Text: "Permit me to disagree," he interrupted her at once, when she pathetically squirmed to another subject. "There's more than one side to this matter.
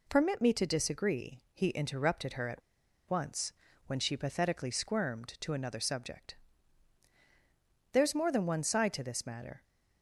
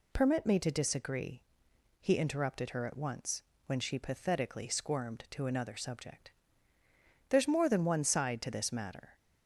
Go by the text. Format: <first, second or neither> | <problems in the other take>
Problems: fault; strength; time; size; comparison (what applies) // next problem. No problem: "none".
second | pauses between "at" and "once"; noticeable; at 2.6 s; 0.48 s long